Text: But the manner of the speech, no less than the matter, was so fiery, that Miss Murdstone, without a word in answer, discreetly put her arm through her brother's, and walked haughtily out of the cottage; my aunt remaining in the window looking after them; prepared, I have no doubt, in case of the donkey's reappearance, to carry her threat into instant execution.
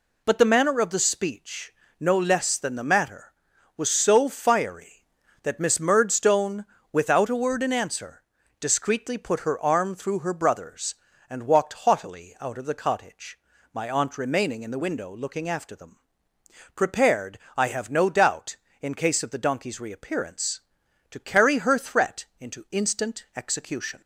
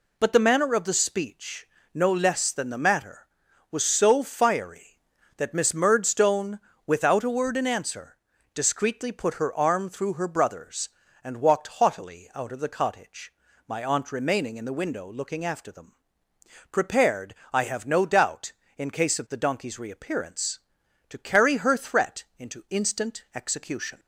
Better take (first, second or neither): neither